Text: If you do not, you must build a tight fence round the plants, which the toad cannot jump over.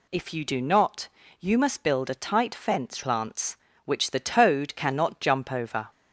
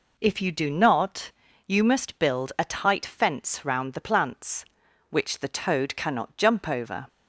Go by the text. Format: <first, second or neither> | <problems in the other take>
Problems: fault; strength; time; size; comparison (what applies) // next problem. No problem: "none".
second | skips "round the"; at 3.0 s